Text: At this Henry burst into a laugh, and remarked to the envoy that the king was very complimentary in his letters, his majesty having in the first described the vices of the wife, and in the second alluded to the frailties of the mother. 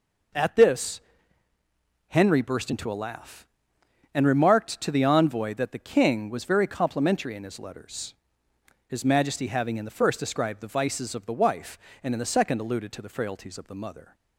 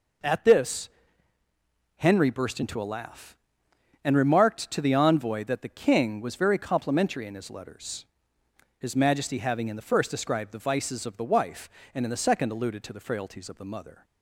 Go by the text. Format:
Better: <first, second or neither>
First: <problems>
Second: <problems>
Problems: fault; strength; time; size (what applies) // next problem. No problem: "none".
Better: neither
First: pauses between "this" and "Henry"; at 1.0 s; 1.0 s long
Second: pauses between "this" and "Henry"; at 0.8 s; 1.0 s long